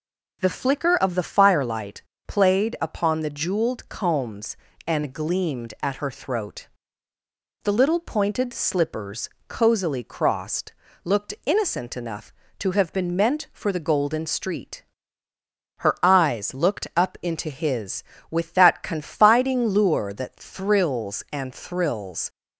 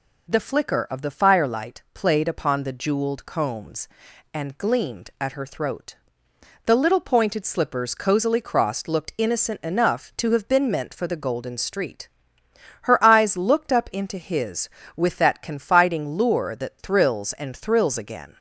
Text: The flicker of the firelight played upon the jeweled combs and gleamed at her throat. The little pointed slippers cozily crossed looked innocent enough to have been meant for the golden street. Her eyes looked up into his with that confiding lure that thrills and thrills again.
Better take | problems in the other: second | pauses between "firelight" and "played"; slight; at 1.9 s; 0.26 s long // pauses between "slippers" and "cozily"; slight; at 9.2 s; 0.20 s long // pauses between "crossed" and "looked"; slight; at 10.7 s; 0.32 s long // stops before "again"; at 22.3 s

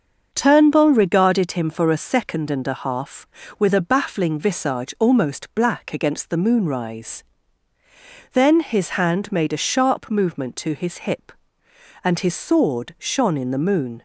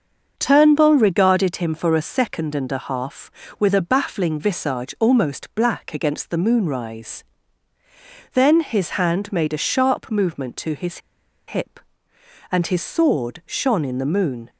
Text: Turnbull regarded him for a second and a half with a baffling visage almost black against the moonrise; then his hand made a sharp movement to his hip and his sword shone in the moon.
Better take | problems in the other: first | starts louder than the rest; until 1.3 s; 6.5 dB; also in the first // pauses between "his" and "hip"; noticeable; at 10.9 s; 0.49 s long

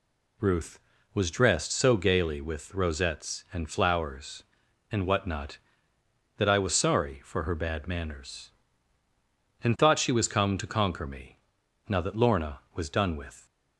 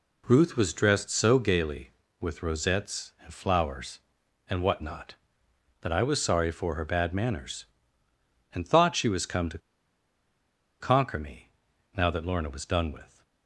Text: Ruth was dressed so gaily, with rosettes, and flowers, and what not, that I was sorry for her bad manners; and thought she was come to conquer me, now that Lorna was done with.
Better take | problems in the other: first | pauses between "to" and "conquer"; at 9.5 s; 1.2 s long

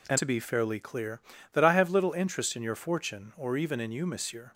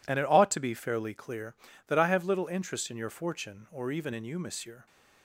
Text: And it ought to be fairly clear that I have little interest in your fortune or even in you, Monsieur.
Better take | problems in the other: second | skips "it ought"; at 0.1 s

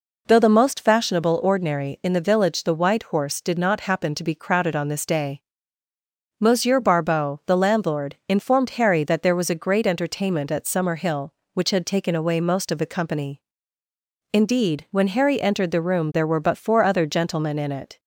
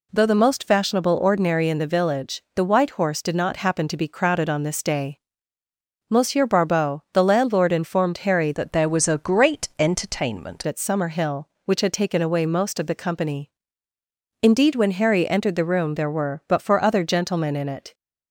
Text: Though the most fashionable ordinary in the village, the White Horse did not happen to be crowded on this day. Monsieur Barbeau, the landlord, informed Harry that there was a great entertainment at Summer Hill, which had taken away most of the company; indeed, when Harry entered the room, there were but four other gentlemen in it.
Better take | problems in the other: first | changes voice from "that" to "entertainment"; from 8.5 to 10.6 s; 2.1 s long

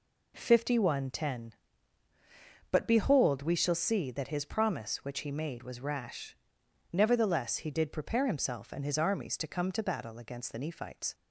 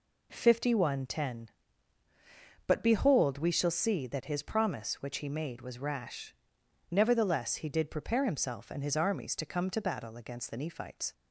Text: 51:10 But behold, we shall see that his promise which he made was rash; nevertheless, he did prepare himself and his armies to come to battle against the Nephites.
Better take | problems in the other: neither | none

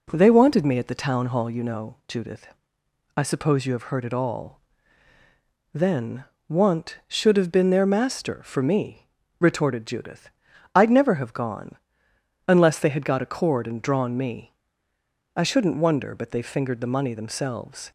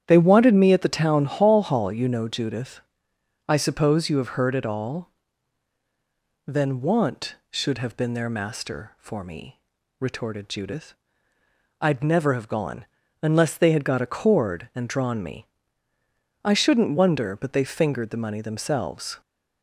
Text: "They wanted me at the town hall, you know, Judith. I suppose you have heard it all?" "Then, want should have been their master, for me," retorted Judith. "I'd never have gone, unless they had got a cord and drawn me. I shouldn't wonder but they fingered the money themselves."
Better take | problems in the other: first | starts louder than the rest; strong; until 1.0 s; 9.5 dB // says "hall" twice; at 1.6 s

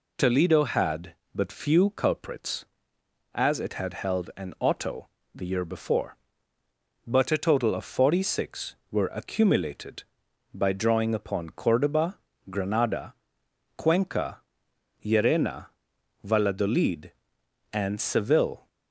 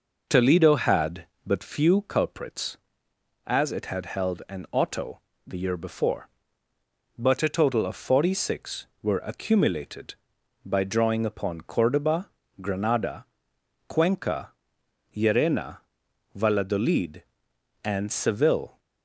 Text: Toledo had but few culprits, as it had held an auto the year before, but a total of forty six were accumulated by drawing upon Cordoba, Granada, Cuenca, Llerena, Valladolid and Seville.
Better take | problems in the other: first | starts louder than the rest; noticeable; until 1.6 s; 5.5 dB // pauses between "auto" and "the"; slight; at 5.1 s; 0.26 s long; slight in the first

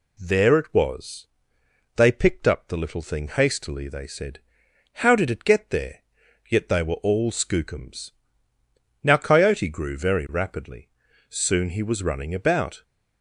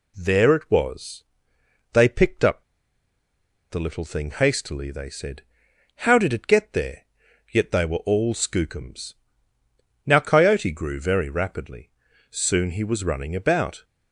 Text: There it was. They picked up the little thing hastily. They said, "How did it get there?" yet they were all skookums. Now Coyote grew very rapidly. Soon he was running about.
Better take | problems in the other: first | pauses between "up" and "the"; at 2.6 s; 1.0 s long

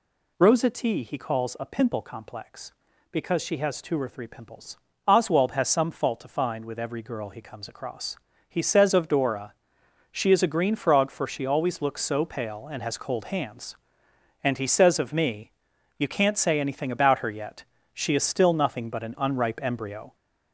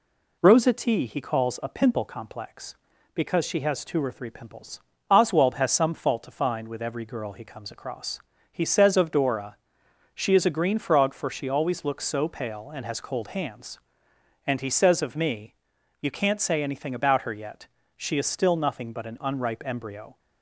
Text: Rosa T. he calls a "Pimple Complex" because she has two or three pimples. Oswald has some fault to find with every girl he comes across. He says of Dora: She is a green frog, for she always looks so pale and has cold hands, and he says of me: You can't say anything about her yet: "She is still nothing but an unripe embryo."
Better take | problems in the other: second | gets louder; noticeable; throughout; 4.5 dB

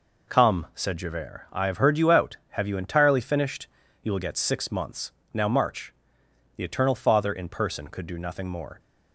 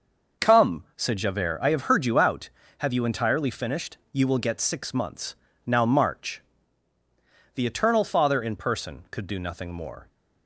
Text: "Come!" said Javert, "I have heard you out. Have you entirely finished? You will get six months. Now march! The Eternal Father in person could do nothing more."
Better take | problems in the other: neither | none

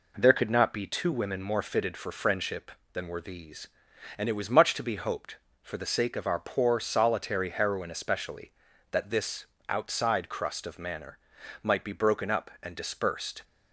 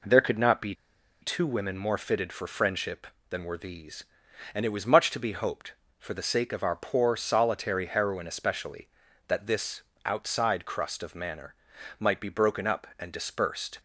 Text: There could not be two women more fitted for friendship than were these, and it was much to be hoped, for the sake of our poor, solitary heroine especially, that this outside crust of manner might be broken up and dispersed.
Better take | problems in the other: first | pauses between "be" and "two"; noticeable; at 0.7 s; 0.48 s long // pauses between "this" and "outside"; slight; at 9.8 s; 0.22 s long; slight in the first // pauses between "manner" and "might"; noticeable; at 11.5 s; 0.46 s long; noticeable in the first

